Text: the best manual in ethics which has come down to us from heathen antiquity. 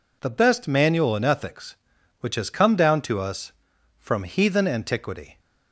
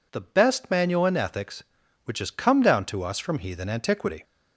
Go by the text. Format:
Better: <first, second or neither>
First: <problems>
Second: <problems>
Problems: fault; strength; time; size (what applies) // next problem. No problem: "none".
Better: neither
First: none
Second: none